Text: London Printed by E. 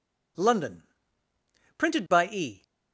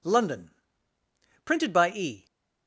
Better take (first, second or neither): neither